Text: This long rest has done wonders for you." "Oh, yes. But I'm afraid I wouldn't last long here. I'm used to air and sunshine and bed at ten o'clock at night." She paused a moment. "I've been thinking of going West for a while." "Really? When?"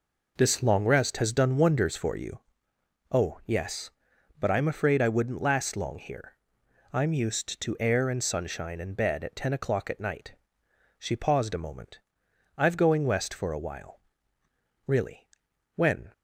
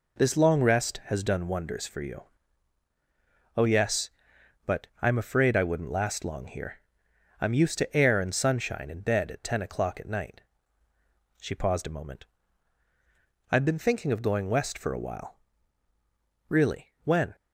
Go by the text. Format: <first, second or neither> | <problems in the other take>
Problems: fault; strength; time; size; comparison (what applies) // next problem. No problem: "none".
second | skips "been thinking of"; at 12.7 s